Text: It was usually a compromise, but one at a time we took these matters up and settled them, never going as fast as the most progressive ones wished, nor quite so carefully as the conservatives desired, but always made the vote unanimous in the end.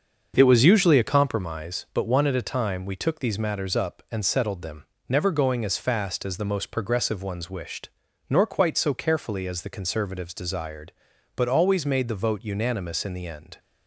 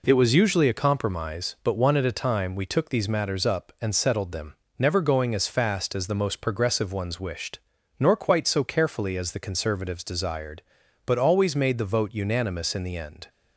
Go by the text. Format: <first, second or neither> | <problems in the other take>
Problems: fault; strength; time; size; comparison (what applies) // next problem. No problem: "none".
second | starts louder than the rest; until 1.4 s; 6.5 dB